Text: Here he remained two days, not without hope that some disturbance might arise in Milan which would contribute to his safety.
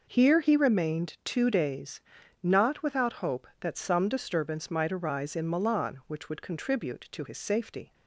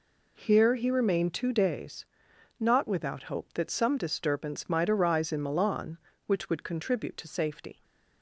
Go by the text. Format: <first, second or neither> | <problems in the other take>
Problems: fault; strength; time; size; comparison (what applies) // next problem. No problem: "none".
first | skips "his"; at 7.2 s